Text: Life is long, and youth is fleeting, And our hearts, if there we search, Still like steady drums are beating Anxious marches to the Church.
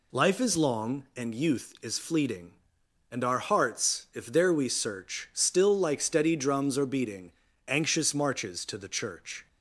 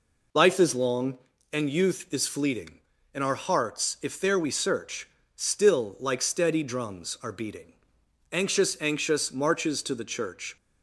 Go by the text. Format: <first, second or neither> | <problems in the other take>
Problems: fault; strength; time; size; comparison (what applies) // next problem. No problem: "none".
first | pauses between "beating" and "Anxious"; noticeable; at 7.7 s; 0.58 s long; slight in the first // says "Anxious" twice; at 8.8 s